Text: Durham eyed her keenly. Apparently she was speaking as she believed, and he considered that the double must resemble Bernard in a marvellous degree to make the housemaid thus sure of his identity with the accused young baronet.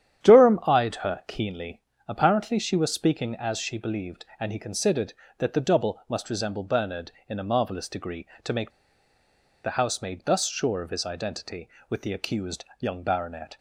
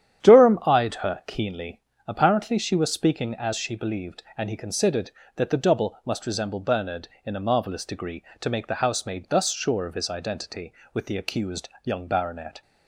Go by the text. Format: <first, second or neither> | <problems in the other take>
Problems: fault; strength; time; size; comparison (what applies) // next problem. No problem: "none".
second | starts louder than the rest; strong; until 1.3 s; 10 dB; strong in the second // pauses between "make" and "the"; noticeable; at 8.6 s; 0.94 s long